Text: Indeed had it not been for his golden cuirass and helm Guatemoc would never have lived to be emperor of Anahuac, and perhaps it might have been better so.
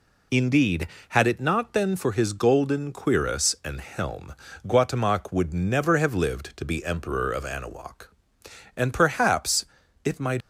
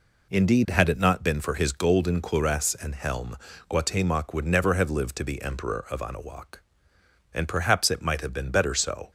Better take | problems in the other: second | pauses between "helm" and "Guatemoc"; slight; at 4.3 s; 0.34 s long; slight in the second // pauses between "perhaps" and "it"; at 9.6 s; 0.40 s long // stops before "have been better so"; at 10.4 s

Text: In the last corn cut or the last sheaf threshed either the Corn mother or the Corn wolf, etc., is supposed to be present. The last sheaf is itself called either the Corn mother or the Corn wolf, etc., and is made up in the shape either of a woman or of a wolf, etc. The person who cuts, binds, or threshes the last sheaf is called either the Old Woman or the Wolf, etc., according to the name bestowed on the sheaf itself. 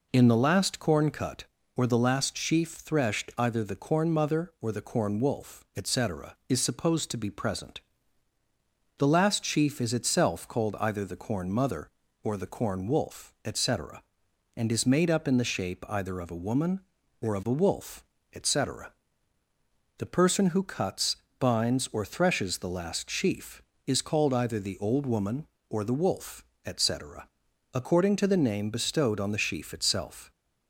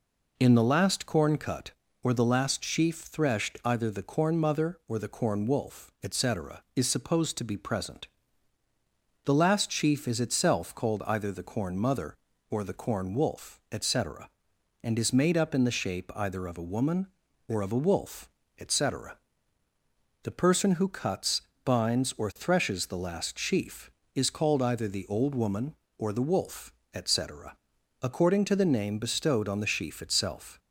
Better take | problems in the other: neither | none

